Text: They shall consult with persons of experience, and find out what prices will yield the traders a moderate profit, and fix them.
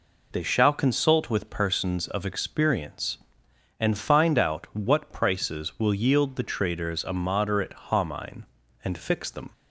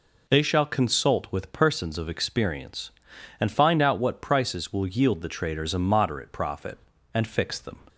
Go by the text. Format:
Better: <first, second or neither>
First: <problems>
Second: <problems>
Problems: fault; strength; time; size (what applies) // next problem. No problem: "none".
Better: second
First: says "homine" for "profit"; at 7.8 s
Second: none